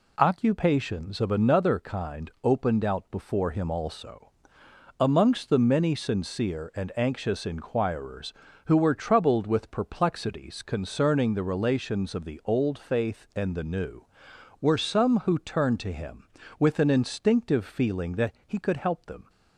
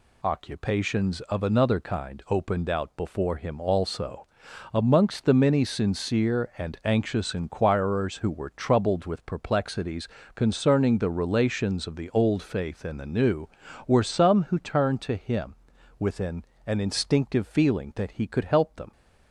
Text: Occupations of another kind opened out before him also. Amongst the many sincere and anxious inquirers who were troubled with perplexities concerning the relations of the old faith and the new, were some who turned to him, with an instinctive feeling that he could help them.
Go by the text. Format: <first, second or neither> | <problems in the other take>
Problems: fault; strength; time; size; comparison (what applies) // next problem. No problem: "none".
first | pauses between "perplexities" and "concerning"; slight; at 10.0 s; 0.28 s long // says "an" twice; at 16.6 s